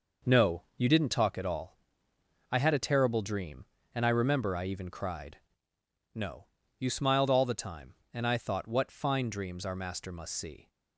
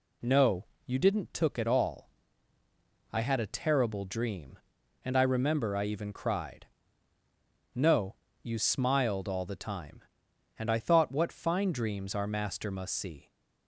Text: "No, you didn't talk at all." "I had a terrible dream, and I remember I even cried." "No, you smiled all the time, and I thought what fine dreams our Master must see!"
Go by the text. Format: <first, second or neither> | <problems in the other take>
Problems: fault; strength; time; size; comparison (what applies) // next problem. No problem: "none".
first | says "took" for "talk"; at 1.3 s